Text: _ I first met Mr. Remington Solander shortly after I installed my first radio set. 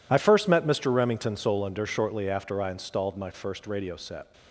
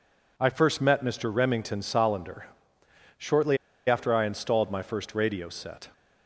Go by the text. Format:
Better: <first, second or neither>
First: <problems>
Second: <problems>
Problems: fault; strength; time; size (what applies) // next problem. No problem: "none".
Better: first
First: none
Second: pauses between "Solander" and "shortly"; noticeable; at 2.4 s; 0.70 s long // pauses between "shortly" and "after"; slight; at 3.5 s; 0.30 s long